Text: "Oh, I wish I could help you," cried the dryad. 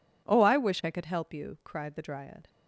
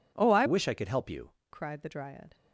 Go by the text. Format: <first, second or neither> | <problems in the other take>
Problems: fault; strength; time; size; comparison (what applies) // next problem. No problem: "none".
first | changes voice from "wish" to "you"; from 0.4 to 1.3 s; 0.9 s long